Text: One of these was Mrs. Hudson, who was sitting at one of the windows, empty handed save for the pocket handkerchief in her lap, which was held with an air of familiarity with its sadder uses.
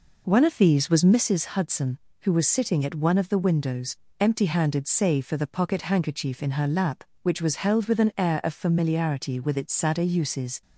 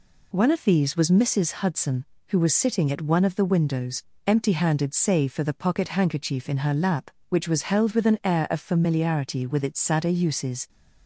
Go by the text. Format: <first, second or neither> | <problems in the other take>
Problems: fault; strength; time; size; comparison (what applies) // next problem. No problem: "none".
second | starts louder than the rest; noticeable; until 1.4 s; 4.5 dB